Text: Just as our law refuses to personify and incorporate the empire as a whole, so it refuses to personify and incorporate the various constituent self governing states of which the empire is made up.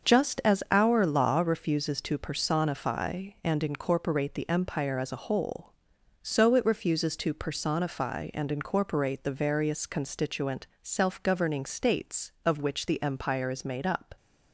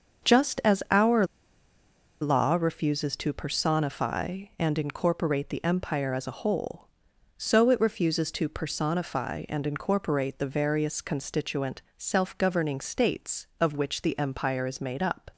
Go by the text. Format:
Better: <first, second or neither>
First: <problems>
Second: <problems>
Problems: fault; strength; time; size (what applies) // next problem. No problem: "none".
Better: first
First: starts louder than the rest; until 1.1 s; 6.5 dB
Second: starts louder than the rest; until 2.3 s; 6.5 dB // pauses between "our" and "law"; noticeable; at 1.2 s; 0.95 s long